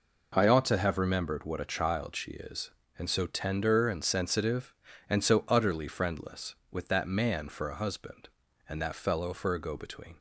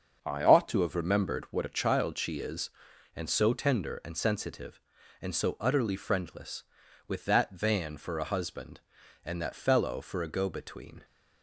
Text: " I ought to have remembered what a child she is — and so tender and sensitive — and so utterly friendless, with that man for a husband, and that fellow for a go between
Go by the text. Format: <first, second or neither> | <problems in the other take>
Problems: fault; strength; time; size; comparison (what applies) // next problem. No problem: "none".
first | starts louder than the rest; until 1.2 s; 6.5 dB // says "van" for "man"; at 7.5 s